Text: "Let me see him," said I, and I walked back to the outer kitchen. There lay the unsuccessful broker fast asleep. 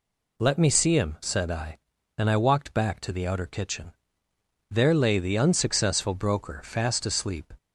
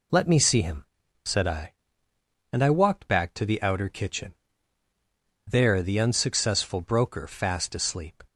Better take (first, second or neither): first